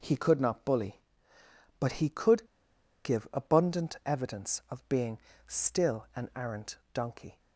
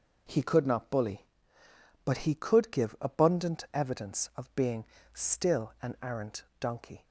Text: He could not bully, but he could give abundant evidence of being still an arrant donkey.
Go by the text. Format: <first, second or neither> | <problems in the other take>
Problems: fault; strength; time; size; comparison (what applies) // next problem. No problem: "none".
second | pauses between "could" and "give"; noticeable; at 2.4 s; 0.58 s long // pauses between "being" and "still"; slight; at 5.1 s; 0.30 s long; slight in the second // pauses between "arrant" and "donkey"; slight; at 6.7 s; 0.16 s long; slight in the second